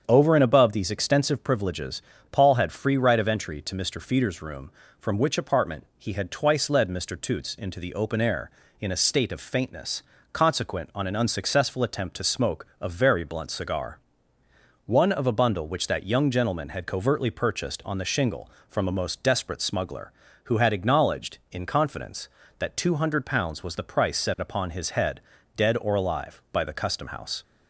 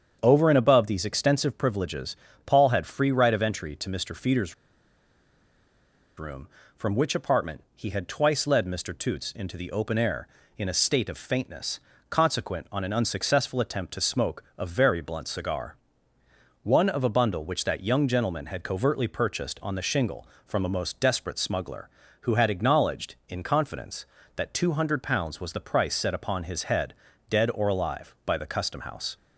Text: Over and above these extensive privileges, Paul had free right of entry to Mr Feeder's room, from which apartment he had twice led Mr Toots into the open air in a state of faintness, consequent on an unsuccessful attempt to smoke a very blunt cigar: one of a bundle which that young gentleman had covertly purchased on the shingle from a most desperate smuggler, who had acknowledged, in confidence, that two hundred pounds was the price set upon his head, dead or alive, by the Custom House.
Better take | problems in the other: first | starts louder than the rest; strong; until 1.2 s; 7.5 dB; strong in the first // pauses between "Feeder's" and "room"; strong; at 4.5 s; 1.6 s long // pauses between "smoke" and "a"; slight; at 14.4 s; 0.16 s long; slight in the first

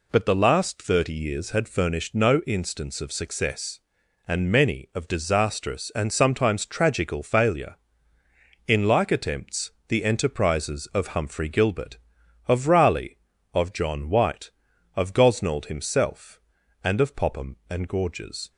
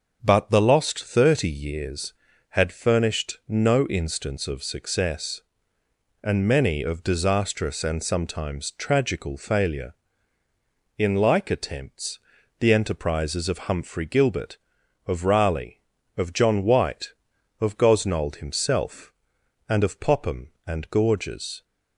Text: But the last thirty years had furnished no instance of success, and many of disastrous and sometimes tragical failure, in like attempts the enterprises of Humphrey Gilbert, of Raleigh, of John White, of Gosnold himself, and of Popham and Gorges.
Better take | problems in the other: first | starts louder than the rest; until 1.2 s; 6.5 dB // says "lost" for "last"; at 0.6 s // pauses between "attempts" and "the"; at 12.1 s; 0.40 s long; slight in the first

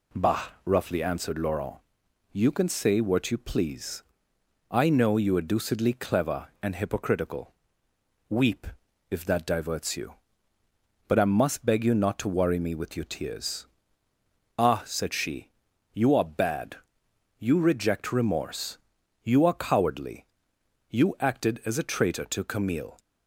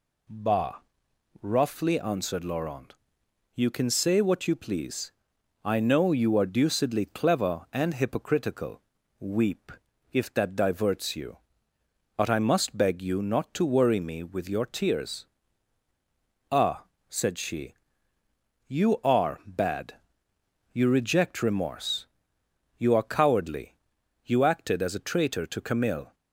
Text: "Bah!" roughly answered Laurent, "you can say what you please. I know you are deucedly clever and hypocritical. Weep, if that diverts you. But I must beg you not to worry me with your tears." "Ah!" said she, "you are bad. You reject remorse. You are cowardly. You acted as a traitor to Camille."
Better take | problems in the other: neither | none

